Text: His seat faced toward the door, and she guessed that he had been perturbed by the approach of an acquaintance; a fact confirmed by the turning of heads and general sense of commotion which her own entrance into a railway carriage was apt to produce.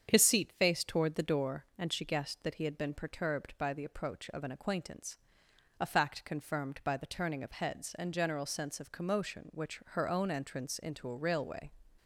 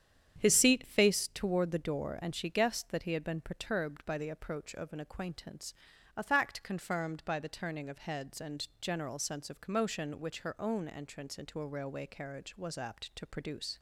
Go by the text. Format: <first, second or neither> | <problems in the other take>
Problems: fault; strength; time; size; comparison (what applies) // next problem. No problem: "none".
second | starts louder than the rest; strong; until 1.1 s; 7.5 dB; strong in the second // stops before "carriage was apt to produce"; at 11.9 s